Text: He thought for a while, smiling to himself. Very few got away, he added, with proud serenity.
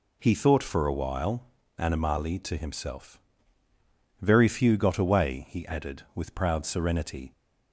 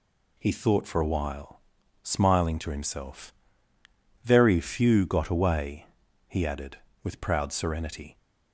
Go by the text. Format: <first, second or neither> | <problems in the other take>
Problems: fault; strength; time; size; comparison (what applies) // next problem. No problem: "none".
second | says "animali" for "smiling"; at 1.7 s